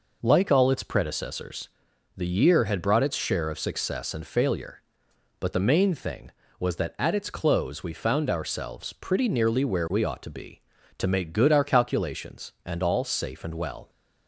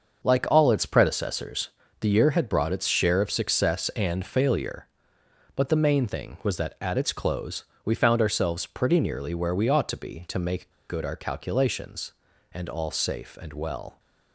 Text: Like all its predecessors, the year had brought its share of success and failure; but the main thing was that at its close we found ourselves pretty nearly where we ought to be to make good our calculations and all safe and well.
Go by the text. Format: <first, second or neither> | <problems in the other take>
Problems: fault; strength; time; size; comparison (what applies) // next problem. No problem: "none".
first | starts louder than the rest; until 1.3 s; 6 dB // pauses between "close" and "we"; slight; at 7.6 s; 0.20 s long // pauses between "make" and "good"; slight; at 10.6 s; 0.19 s long